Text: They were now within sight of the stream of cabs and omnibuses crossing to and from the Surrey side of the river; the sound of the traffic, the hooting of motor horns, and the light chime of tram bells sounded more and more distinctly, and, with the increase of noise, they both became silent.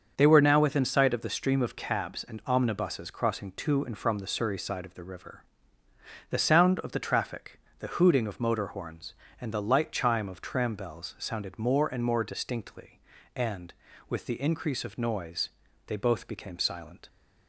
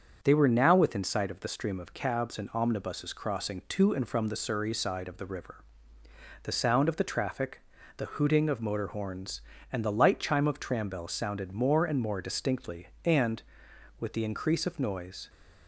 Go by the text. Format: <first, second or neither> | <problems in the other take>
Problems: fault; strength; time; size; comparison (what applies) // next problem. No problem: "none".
first | starts louder than the rest; until 1.2 s; 7 dB; also in the first // stops before "they both became silent"; at 15.2 s